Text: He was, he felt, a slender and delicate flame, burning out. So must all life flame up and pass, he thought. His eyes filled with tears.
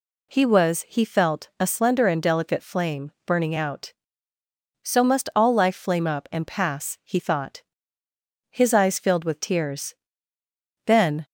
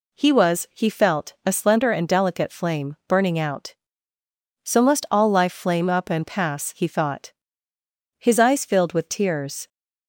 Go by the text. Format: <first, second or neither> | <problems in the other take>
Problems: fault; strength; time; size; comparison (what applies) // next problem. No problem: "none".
second | goes on to say "Then"; slight; from 10.8 s on; 0.40 s long